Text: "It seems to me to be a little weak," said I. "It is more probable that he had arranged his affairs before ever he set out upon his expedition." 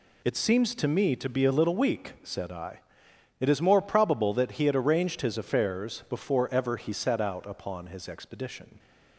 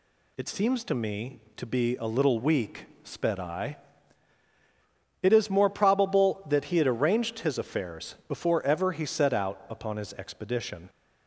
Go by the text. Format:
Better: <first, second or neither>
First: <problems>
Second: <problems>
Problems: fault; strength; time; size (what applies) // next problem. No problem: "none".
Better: first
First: none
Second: says "sped" for "said"; at 3.0 s